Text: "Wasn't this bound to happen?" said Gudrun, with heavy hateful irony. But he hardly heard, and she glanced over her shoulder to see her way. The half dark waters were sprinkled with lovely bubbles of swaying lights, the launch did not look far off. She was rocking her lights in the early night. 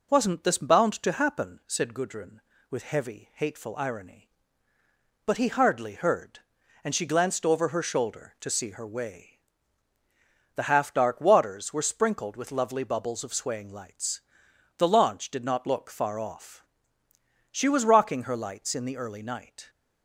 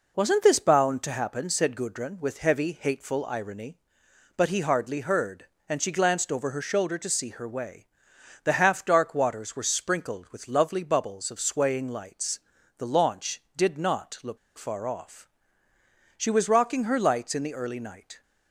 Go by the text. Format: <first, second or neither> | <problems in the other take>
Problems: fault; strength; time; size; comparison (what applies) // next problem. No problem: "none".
first | pauses between "look" and "far"; slight; at 14.3 s; 0.19 s long